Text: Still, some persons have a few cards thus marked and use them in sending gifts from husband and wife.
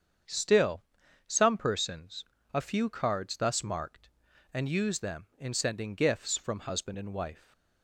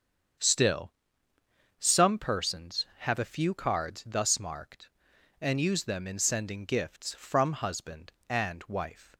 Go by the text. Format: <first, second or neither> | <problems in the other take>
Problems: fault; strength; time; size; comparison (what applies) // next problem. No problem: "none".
second | starts louder than the rest; strong; until 1.7 s; 7.5 dB; strong in the second // skips "have"; at 2.3 s